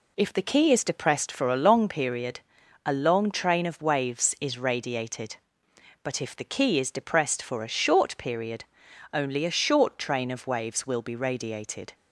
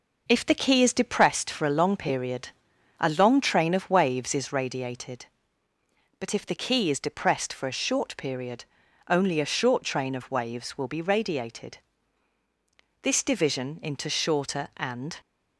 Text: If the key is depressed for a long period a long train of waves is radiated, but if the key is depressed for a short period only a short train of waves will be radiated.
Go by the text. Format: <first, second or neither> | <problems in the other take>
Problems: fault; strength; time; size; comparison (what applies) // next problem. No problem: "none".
first | pauses between "period" and "a"; noticeable; at 2.4 s; 0.50 s long; noticeable in the first // pauses between "period" and "only"; at 8.6 s; 0.44 s long; noticeable in the first // goes on to say "This division into shorter and"; strong; from 13.0 s on; 2.1 s long